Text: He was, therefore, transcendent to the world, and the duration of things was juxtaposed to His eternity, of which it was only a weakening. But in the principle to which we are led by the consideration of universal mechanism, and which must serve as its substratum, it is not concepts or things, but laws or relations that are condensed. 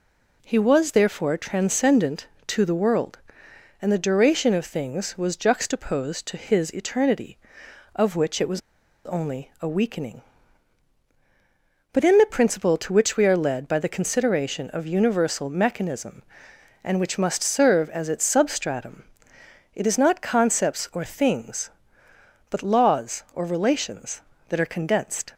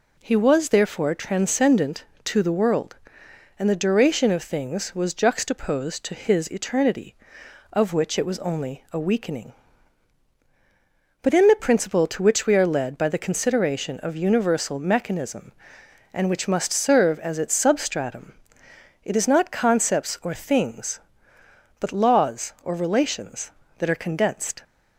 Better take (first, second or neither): second